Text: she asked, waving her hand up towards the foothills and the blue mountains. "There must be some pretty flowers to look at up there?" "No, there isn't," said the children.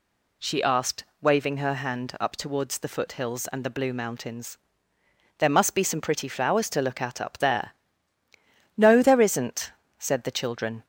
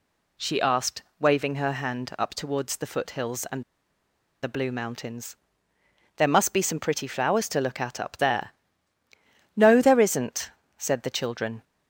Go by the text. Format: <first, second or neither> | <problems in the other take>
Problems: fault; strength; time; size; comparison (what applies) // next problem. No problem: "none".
first | pauses between "and" and "the"; noticeable; at 3.6 s; 0.79 s long